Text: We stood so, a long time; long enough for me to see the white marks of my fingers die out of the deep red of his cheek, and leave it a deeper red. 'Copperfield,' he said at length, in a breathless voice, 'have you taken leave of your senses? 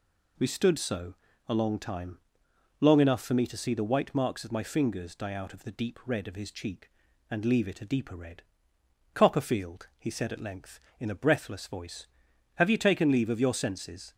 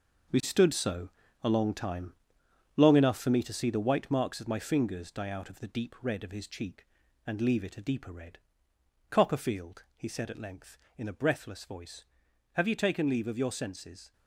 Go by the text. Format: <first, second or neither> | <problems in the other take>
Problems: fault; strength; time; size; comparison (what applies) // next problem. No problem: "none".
first | gets quieter; strong; throughout; 9.5 dB